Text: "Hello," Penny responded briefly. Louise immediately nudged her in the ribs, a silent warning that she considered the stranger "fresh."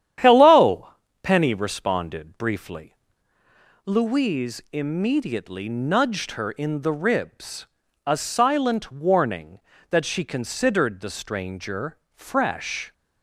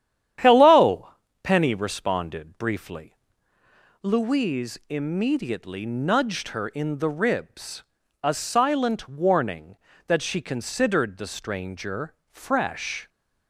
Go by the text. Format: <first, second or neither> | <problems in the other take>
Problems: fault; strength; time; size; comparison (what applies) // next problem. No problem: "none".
neither | starts louder than the rest; strong; the same in both // pauses between "stranger" and "fresh"; slight; the same in both